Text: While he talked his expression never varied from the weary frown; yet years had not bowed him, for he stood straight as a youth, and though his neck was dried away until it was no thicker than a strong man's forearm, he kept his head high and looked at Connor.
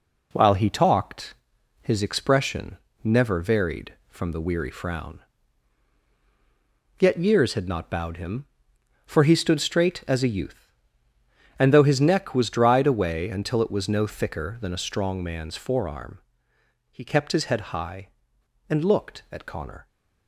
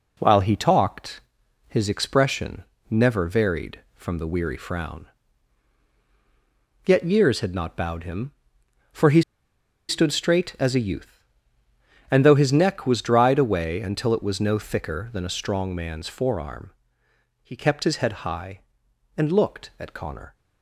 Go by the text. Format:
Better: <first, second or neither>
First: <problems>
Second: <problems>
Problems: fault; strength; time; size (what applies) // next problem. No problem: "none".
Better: first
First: pauses between "talked" and "his"; noticeable; at 1.3 s; 0.48 s long // pauses between "expression" and "never"; slight; at 2.7 s; 0.26 s long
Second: pauses between "talked" and "his"; noticeable; at 1.2 s; 0.48 s long // pauses between "expression" and "never"; slight; at 2.6 s; 0.26 s long // pauses between "he" and "stood"; noticeable; at 9.2 s; 0.67 s long